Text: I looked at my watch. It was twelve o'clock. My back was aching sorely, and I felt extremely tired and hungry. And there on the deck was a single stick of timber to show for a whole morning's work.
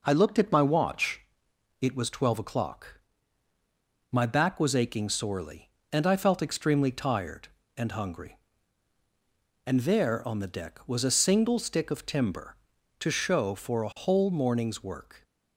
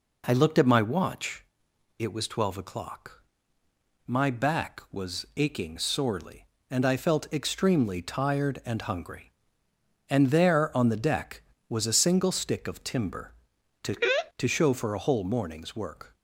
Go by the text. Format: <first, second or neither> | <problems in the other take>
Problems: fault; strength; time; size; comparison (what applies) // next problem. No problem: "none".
first | says "to" twice; at 14.3 s